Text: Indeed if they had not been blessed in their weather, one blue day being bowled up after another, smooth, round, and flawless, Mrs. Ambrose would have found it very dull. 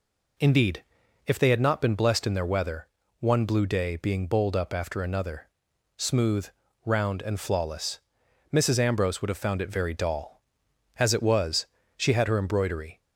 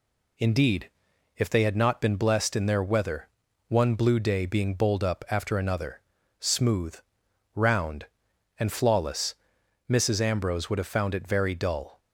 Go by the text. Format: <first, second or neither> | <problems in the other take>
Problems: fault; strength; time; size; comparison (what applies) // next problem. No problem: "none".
second | pauses between "Indeed" and "if"; at 0.8 s; 0.44 s long; noticeable in the second // goes on to say "As it was she had her embroidery"; strong; from 10.9 s on; 2.0 s long